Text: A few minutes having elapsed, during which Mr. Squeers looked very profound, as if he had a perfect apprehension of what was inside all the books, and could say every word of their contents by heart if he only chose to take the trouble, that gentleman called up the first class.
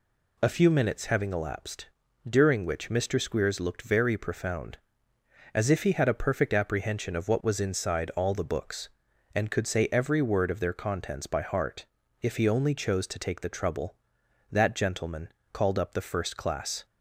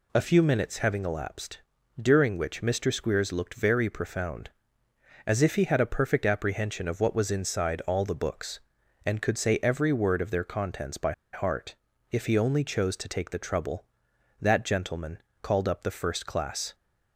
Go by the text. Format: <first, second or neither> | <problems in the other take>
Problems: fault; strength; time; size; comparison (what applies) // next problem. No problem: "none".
first | pauses between "by" and "heart"; slight; at 11.1 s; 0.21 s long // pauses between "heart" and "if"; slight; at 11.7 s; 0.34 s long; slight in the first // pauses between "gentleman" and "called"; slight; at 15.1 s; 0.24 s long; slight in the first